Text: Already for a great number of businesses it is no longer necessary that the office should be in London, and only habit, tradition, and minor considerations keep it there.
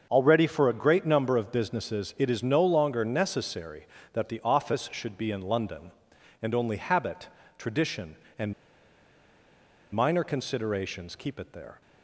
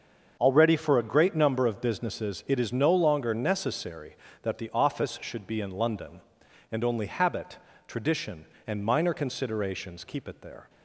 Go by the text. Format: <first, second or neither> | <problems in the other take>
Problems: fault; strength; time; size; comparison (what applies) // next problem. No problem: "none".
second | starts louder than the rest; until 1.1 s; 6.5 dB; also in the second // pauses between "and" and "minor"; strong; at 8.5 s; 1.4 s long